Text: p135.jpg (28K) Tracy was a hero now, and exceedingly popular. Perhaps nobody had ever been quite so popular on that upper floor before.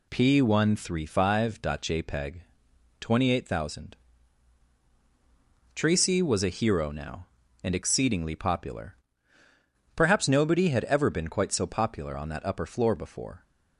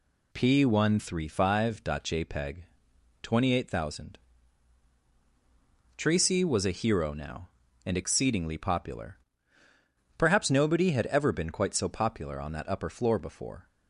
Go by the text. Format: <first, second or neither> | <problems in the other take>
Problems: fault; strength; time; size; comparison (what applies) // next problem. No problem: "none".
neither | none